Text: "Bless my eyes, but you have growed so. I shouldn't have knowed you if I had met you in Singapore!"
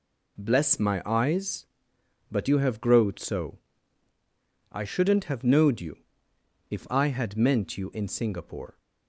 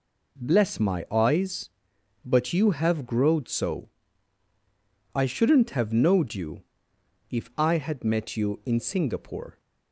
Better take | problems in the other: second | pauses between "you" and "if"; noticeable; at 5.9 s; 0.72 s long; noticeable in the second // says "meant" for "met"; at 7.3 s

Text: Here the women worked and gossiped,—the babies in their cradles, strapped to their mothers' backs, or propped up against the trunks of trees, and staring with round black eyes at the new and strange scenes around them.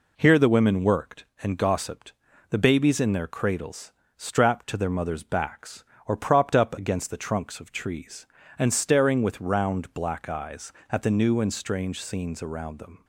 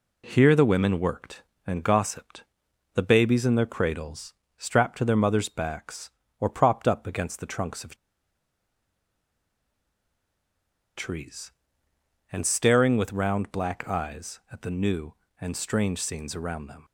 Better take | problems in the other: first | pauses between "of" and "trees"; strong; at 7.9 s; 3.0 s long

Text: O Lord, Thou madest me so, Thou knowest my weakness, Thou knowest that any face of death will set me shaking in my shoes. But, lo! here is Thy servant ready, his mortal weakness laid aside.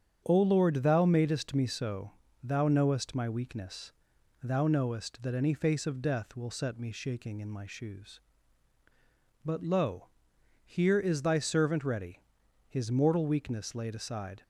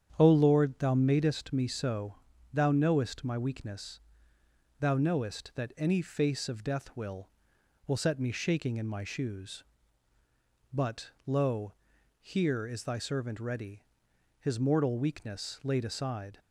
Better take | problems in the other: first | starts louder than the rest; strong; until 1.1 s; 8.5 dB; strong in the first // says "will" twice; at 7.8 s

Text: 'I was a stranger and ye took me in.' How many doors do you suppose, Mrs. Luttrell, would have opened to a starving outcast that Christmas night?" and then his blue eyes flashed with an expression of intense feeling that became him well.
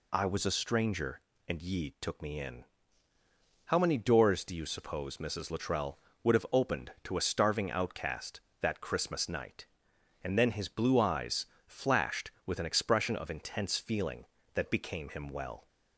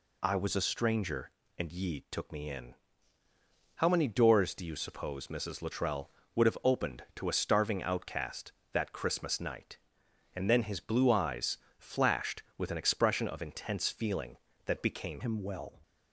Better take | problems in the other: first | pauses between "eyes" and "flashed"; slight; at 11.5 s; 0.22 s long; slight in the first // changes voice at "him"; from 15.2 s on; 0.5 s long

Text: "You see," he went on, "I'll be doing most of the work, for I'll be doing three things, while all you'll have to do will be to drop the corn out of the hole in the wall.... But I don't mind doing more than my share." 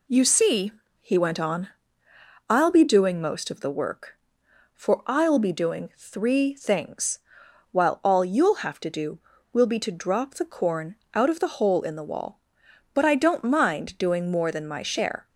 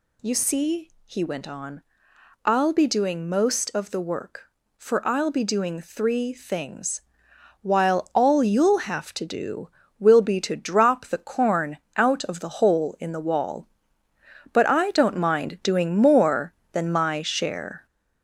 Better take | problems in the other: first | gets louder; noticeable; throughout; 5 dB // pauses between "corn" and "out"; slight; at 11.7 s; 0.18 s long; slight in the first

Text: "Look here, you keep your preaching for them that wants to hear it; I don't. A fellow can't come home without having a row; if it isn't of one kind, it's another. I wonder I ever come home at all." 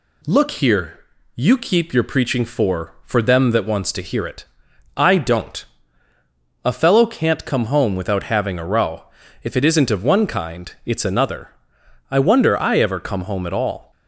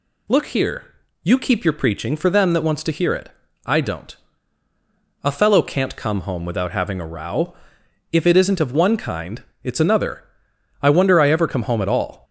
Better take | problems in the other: second | says "for" twice; at 3.0 s

